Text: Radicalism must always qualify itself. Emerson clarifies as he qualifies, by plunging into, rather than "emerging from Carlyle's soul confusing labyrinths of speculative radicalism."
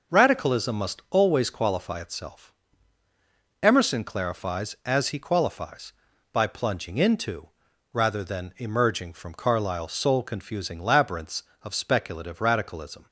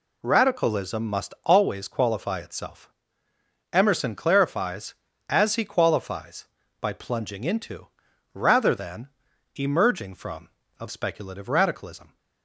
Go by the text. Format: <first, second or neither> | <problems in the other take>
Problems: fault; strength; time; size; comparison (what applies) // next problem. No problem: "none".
first | pauses between "than" and "emerging"; noticeable; at 9.0 s; 0.48 s long // skips "Carlyle's soul confusing labyrinths"; at 10.6 s